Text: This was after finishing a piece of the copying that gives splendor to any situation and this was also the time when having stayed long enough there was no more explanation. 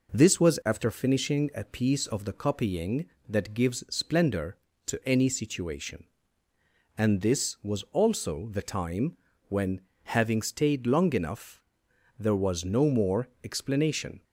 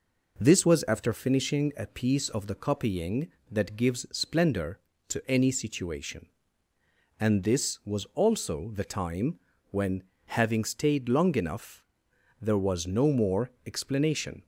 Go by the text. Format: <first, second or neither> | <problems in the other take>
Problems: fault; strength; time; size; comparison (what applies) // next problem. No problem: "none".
neither | pauses between "time" and "when"; slight; the same in both // pauses between "when" and "having"; slight; the same in both // pauses between "enough" and "there"; noticeable; the same in both // pauses between "more" and "explanation"; slight; the same in both